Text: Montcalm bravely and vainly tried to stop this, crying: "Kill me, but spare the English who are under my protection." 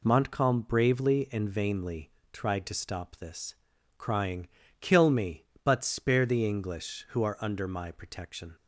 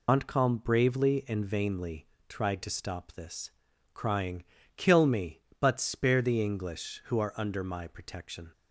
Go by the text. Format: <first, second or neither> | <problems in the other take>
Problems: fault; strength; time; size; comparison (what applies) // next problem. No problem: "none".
first | loses the start of "Montcalm"; at 0.0 s; 100 ms // pauses between "vainly" and "tried"; slight; at 2.0 s; 0.22 s long; slight in the first